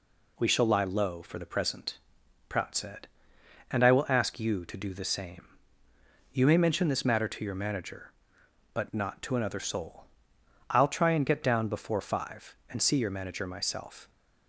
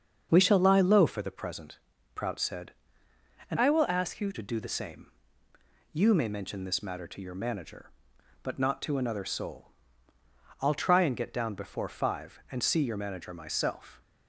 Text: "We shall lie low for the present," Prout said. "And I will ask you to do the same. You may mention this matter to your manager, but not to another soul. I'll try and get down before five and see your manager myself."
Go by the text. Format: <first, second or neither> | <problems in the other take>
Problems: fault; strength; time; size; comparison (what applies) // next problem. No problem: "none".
first | starts louder than the rest; until 1.3 s; 7 dB // changes voice from "I" to "you"; from 3.5 to 4.3 s; 0.8 s long